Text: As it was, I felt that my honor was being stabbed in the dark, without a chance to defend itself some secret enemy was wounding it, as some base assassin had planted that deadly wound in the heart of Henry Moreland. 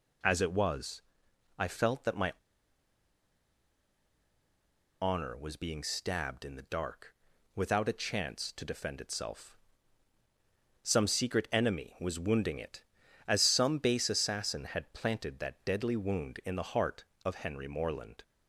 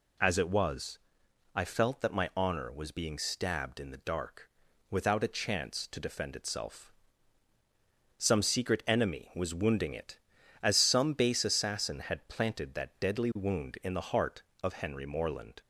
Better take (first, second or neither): second